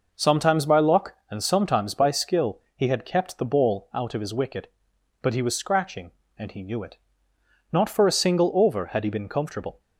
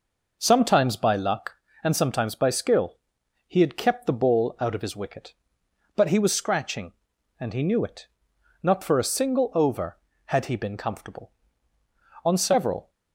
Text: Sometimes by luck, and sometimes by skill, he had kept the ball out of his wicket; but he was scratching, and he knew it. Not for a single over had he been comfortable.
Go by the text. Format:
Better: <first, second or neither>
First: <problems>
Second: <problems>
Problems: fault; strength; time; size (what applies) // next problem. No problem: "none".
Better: first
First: none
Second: goes on to say "On several"; noticeable; from 12.2 s on; 0.66 s long